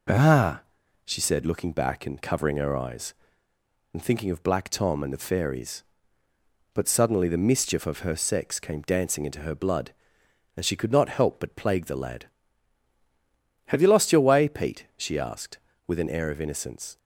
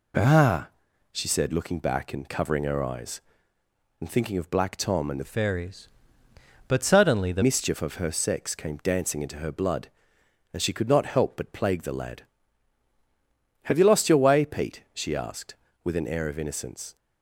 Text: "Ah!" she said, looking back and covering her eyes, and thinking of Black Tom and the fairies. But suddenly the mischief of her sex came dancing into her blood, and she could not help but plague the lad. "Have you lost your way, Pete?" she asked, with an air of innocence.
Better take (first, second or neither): first